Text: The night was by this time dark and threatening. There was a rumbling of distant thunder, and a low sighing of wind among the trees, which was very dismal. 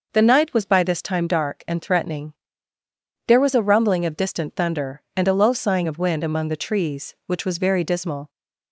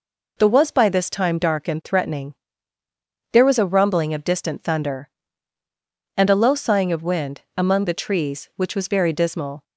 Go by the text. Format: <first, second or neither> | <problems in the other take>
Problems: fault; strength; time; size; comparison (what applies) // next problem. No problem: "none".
first | skips "night"; at 0.4 s // pauses between "wind" and "among"; slight; at 7.4 s; 0.16 s long